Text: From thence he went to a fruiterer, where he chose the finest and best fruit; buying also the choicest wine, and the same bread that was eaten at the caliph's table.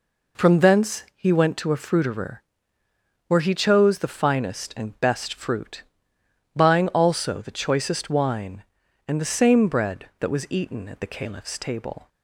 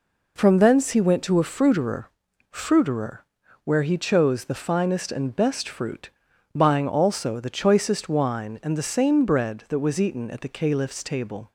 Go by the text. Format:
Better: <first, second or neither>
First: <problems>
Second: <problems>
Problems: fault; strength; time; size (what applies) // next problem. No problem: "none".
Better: first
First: none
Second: says "fruiterer" twice; at 2.5 s